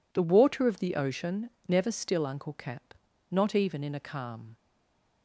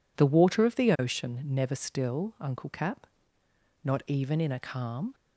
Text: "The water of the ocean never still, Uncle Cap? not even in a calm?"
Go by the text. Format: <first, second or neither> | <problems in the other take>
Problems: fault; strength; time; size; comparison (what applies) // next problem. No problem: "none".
second | pauses between "ocean" and "never"; slight; at 1.5 s; 0.16 s long // stays silent after the last word; slight; from 4.5 s on; 0.7 s long